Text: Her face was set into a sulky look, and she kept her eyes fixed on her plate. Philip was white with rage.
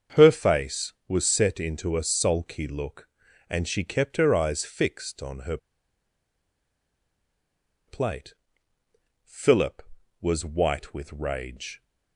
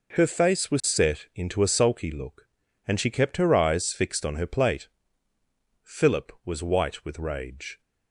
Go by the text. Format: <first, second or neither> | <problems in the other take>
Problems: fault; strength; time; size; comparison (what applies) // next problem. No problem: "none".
second | starts louder than the rest; strong; until 1.3 s; 7 dB // pauses between "her" and "plate"; strong; at 5.5 s; 2.3 s long